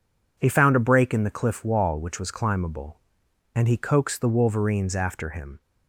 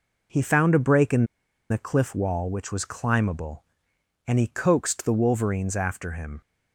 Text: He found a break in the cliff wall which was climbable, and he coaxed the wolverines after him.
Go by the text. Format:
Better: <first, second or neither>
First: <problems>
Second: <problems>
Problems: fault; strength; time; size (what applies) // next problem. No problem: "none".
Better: first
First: none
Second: pauses between "in" and "the"; at 1.2 s; 0.45 s long